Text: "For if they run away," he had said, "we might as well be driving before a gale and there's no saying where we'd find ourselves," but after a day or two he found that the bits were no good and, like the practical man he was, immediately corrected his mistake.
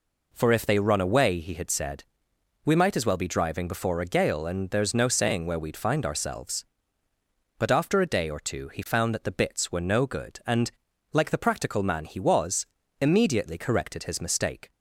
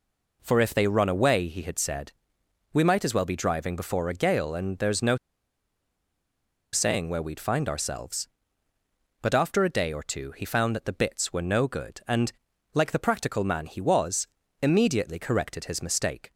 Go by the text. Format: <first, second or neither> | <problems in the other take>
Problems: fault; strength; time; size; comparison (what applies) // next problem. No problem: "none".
first | pauses between "no" and "saying"; strong; at 5.1 s; 1.5 s long